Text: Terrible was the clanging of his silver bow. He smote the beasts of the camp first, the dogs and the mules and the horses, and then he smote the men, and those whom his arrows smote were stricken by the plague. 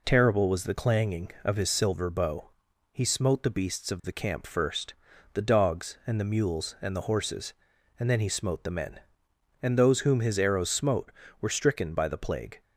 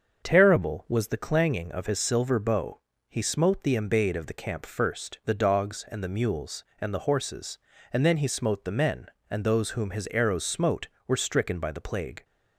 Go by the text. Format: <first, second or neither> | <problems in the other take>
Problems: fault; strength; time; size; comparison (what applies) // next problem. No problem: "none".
first | starts louder than the rest; until 1.2 s; 6.5 dB // says "embayed" for "beasts"; at 3.7 s